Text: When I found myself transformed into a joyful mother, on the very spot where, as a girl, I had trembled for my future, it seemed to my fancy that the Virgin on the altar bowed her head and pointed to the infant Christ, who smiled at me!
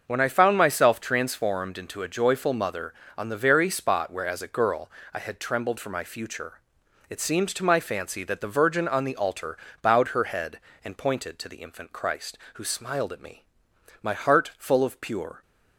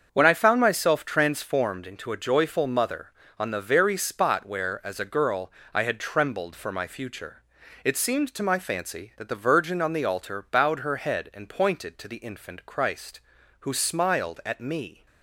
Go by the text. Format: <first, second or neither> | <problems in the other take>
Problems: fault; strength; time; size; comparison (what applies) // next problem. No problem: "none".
second | starts louder than the rest; until 1.0 s; 6.5 dB; also in the second // pauses between "altar" and "bowed"; slight; at 9.5 s; 0.24 s long // goes on to say "My heart full of pure"; from 14.0 s on; 1.3 s long